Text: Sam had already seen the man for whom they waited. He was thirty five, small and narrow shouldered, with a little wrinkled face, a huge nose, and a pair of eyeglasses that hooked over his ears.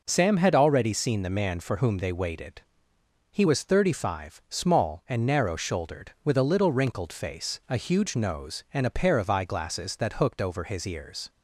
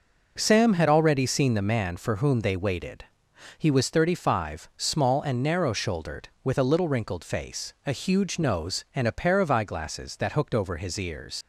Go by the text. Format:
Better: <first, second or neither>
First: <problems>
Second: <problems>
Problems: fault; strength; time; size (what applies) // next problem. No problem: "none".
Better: first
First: none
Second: leaves "ears" unfinished; at 11.4 s; 110 ms